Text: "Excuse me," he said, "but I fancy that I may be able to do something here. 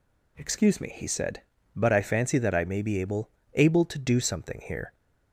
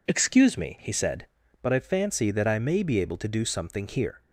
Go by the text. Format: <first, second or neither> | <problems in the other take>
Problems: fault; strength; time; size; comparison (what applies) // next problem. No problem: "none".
second | says "able" twice; at 3.5 s